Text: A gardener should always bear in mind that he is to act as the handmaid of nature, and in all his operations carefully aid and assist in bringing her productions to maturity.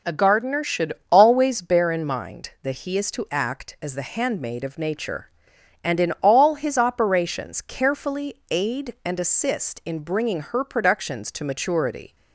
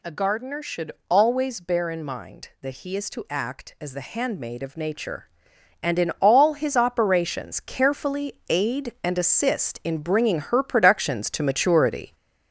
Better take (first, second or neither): first